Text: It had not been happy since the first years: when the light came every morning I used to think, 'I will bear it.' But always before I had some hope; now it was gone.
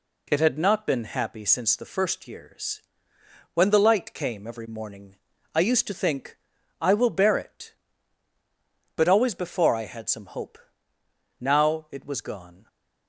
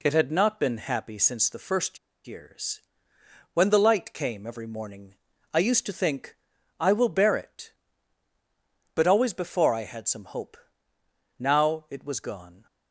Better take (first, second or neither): first